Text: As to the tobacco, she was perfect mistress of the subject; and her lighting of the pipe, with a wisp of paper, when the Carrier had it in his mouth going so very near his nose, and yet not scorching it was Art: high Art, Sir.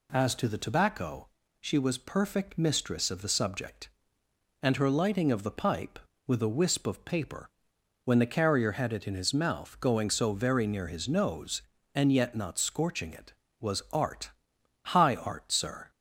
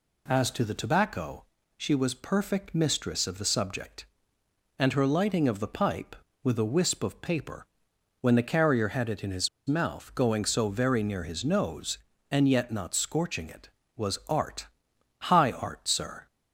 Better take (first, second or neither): first